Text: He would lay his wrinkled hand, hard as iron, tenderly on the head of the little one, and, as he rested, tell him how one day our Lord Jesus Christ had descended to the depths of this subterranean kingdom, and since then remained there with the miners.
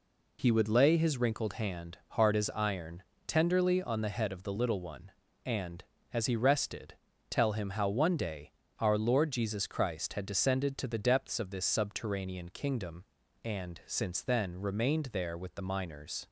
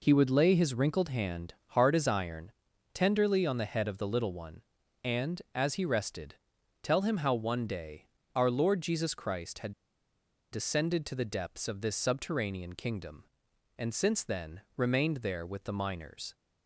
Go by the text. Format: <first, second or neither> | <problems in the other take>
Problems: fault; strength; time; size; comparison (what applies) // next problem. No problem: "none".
first | pauses between "day" and "our"; slight; at 8.0 s; 0.28 s long; slight in the first // pauses between "had" and "descended"; noticeable; at 9.7 s; 0.81 s long